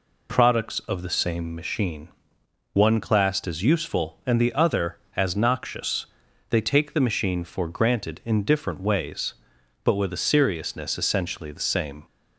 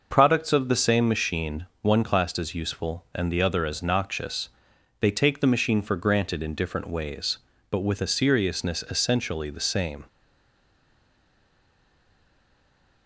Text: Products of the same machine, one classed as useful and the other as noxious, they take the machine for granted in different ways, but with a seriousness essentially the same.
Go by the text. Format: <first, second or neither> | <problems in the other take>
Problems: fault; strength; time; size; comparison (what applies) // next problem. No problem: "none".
first | stays silent after the last word; strong; from 10.0 s on; 3.0 s long